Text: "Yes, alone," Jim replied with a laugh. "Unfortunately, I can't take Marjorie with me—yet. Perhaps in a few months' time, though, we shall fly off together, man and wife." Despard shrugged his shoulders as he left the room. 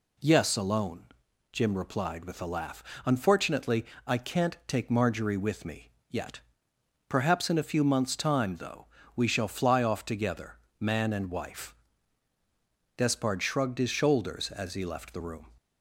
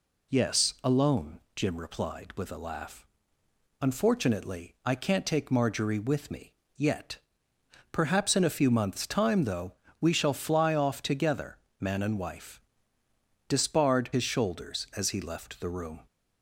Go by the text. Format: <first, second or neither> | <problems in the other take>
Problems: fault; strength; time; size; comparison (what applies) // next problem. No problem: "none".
first | skips "shrugged"; at 14.1 s